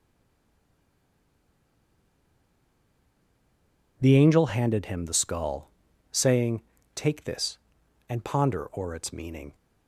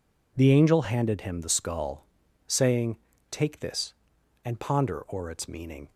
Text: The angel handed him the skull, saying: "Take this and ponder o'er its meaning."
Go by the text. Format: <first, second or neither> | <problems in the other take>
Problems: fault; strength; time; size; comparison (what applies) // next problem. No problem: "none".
second | stays silent before the first word; strong; until 3.9 s; 3.9 s long